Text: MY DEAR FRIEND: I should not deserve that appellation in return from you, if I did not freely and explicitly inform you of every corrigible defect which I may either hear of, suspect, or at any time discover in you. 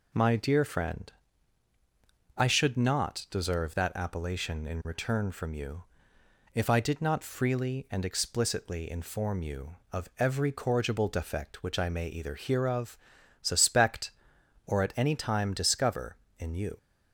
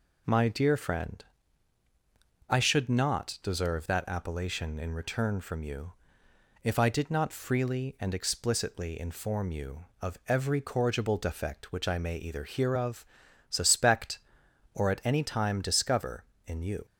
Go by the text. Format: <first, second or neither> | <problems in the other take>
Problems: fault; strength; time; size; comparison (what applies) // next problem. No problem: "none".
neither | none